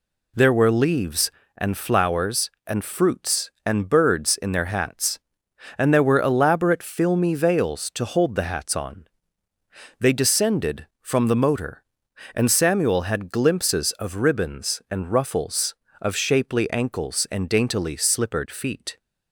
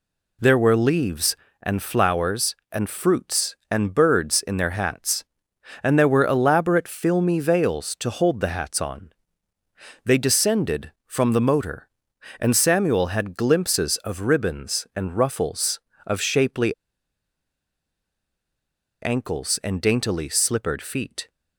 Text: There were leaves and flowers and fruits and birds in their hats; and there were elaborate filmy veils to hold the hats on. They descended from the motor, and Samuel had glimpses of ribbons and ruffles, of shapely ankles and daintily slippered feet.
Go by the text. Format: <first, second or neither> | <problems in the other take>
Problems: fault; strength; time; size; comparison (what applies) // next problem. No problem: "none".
first | pauses between "shapely" and "ankles"; strong; at 16.7 s; 2.2 s long